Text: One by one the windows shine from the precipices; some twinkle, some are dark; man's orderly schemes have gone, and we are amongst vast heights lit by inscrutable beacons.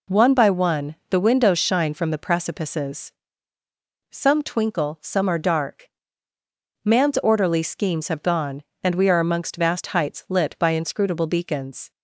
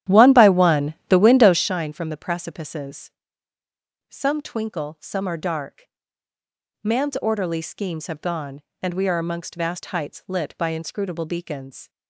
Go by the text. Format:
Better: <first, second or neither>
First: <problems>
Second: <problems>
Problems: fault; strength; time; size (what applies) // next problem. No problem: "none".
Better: first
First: pauses between "one" and "the"; slight; at 0.9 s; 0.16 s long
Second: starts louder than the rest; strong; until 1.7 s; 11.5 dB // pauses between "one" and "the"; slight; at 0.9 s; 0.16 s long